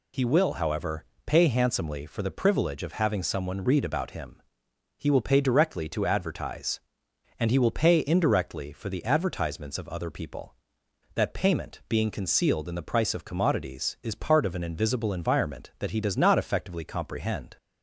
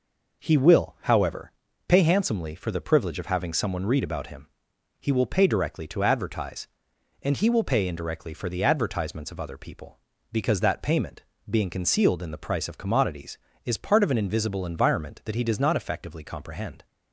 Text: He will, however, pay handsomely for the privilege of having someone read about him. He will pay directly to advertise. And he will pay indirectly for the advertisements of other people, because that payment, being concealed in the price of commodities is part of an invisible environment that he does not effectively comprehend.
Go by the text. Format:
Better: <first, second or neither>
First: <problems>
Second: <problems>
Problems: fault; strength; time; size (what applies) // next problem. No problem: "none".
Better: second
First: skips "because"; at 10.8 s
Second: none